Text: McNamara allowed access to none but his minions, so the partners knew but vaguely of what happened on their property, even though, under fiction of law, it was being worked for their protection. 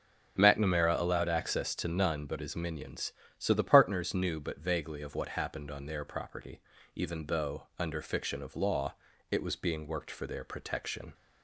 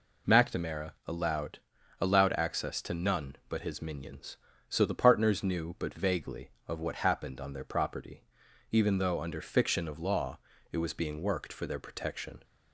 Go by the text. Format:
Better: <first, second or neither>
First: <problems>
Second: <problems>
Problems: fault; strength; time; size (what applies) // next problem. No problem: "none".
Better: first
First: none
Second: says "allowed" twice; at 1.9 s